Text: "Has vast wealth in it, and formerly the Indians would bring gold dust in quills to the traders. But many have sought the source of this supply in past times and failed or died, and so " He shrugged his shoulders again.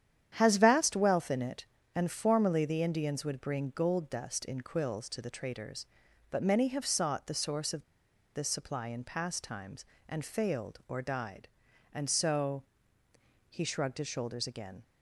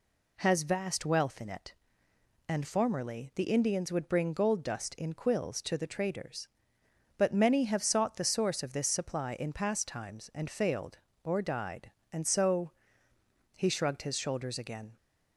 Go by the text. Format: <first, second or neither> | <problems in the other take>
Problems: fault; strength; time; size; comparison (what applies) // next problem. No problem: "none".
second | starts louder than the rest; strong; until 1.3 s; 9.5 dB // pauses between "of" and "this"; noticeable; at 7.8 s; 0.51 s long